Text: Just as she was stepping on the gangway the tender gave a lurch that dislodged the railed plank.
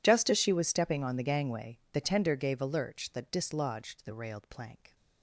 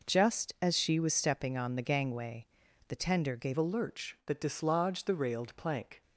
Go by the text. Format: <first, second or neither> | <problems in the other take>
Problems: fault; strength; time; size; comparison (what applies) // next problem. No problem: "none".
first | pauses between "gangway" and "the"; at 2.4 s; 0.42 s long // changes voice at "a"; from 3.5 s on; 2.5 s long